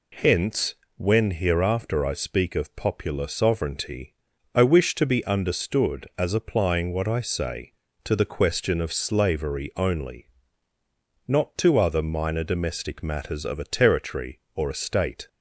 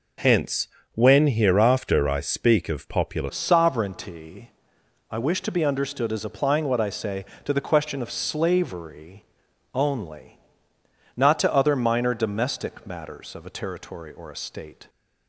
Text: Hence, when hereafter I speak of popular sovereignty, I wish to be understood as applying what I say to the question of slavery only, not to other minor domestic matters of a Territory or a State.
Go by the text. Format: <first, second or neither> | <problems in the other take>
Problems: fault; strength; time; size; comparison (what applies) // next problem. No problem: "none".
first | changes voice at "sovereignty"; from 3.2 s on; 11.6 s long // pauses between "slavery" and "only"; noticeable; at 9.2 s; 0.52 s long